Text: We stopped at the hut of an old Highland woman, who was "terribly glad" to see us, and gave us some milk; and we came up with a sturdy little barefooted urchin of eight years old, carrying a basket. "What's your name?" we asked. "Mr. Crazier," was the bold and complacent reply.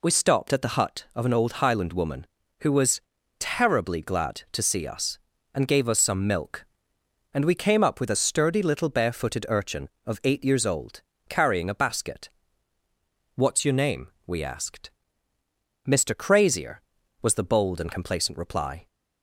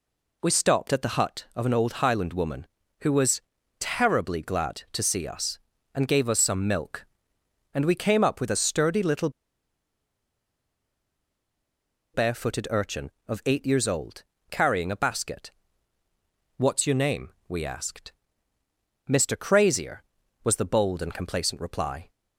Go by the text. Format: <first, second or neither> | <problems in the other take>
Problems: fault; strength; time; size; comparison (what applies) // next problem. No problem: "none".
first | pauses between "was" and "terribly"; at 3.3 s; 0.40 s long; also in the first // pauses between "little" and "barefooted"; strong; at 9.2 s; 2.8 s long